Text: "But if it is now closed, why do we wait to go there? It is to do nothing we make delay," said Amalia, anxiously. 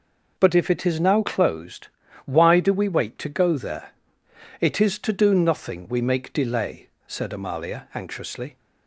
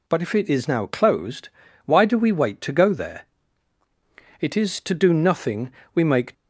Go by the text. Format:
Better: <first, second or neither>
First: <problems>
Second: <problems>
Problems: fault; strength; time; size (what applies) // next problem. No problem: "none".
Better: first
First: none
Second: pauses between "nothing" and "we"; slight; at 5.7 s; 0.24 s long // stops before "delay said Amalia anxiously"; at 6.3 s